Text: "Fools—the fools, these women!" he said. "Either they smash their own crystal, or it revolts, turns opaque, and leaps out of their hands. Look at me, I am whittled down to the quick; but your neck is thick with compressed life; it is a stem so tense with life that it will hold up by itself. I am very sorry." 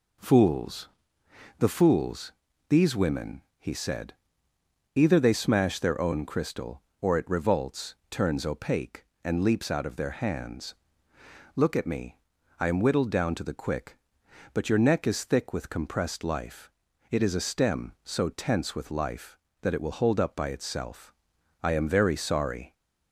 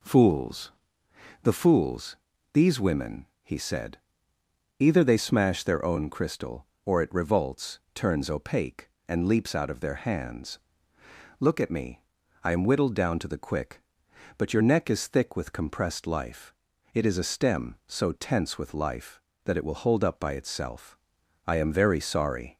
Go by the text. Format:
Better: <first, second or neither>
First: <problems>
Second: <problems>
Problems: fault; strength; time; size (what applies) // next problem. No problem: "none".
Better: neither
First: none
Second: none